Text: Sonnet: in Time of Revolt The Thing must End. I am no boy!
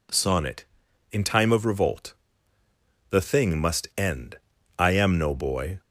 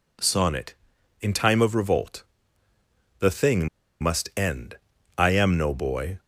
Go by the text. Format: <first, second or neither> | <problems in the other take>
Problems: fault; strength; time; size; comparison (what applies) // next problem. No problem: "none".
first | pauses between "Revolt" and "The"; noticeable; at 2.2 s; 0.96 s long; noticeable in the first // pauses between "Thing" and "must"; slight; at 3.6 s; 0.33 s long